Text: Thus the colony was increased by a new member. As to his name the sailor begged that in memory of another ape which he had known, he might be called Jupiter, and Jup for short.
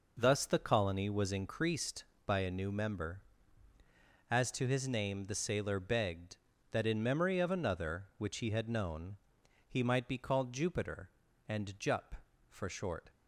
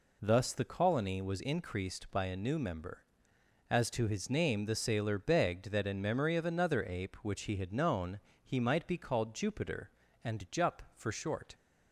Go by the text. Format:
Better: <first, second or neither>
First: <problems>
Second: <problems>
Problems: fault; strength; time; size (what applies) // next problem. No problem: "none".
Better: second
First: skips "ape"; at 8.1 s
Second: none